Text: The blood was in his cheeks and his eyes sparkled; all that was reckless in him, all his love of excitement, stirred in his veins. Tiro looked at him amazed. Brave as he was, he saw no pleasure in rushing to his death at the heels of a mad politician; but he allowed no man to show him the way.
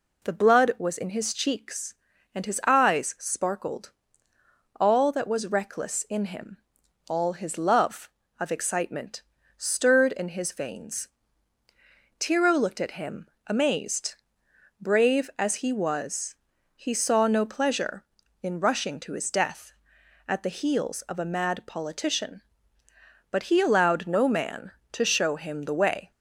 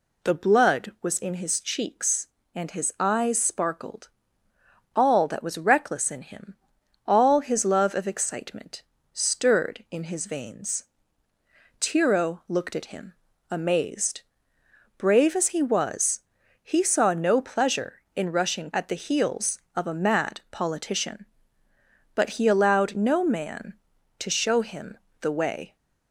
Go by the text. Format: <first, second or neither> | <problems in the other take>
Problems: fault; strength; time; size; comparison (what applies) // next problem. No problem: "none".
first | pauses between "him" and "amazed"; slight; at 13.1 s; 0.36 s long; slight in the first // skips "to his death"; at 18.7 s // pauses between "him" and "the"; slight; at 24.9 s; 0.24 s long